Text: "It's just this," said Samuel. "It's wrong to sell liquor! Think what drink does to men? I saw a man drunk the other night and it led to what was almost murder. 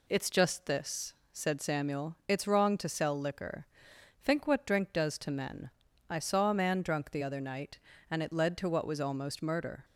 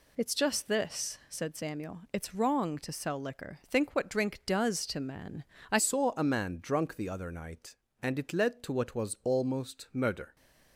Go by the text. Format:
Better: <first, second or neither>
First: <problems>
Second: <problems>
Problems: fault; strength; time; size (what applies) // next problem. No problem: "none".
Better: first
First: none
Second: changes voice at "saw"; from 5.7 s on; 4.6 s long